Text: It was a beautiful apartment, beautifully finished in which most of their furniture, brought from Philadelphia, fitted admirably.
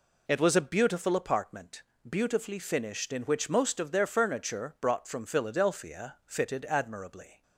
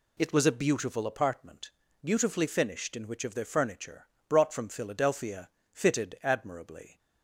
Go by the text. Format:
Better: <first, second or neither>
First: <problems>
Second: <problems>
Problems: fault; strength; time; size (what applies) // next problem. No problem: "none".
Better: first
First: none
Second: skips "most"; at 3.2 s